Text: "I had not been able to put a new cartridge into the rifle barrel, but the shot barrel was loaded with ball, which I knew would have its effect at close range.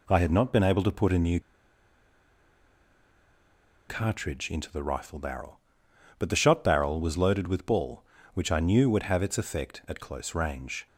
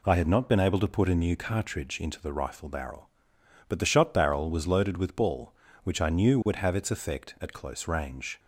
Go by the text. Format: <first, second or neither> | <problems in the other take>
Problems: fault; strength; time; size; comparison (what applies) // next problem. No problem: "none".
second | pauses between "new" and "cartridge"; strong; at 1.3 s; 2.4 s long